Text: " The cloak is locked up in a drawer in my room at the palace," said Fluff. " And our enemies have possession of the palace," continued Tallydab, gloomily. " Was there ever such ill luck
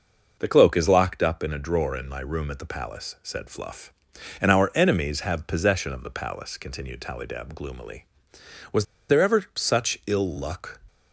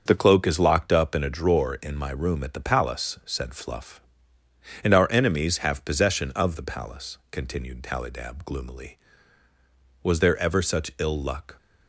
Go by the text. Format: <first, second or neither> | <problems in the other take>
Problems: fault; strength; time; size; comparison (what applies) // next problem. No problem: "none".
second | starts louder than the rest; until 1.3 s; 6 dB; also in the second // pauses between "Was" and "there"; slight; at 8.8 s; 0.24 s long